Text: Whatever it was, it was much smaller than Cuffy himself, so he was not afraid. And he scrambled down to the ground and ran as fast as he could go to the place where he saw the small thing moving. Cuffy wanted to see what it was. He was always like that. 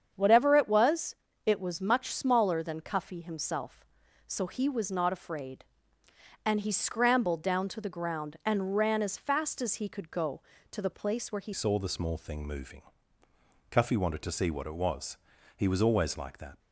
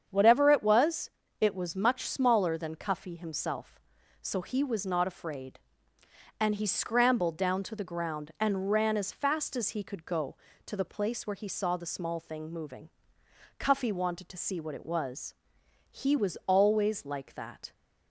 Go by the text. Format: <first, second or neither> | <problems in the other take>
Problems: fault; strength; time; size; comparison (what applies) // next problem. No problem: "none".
second | starts louder than the rest; strong; until 1.1 s; 7.5 dB; strong in the second // changes voice at "saw"; from 11.5 s on; 5.0 s long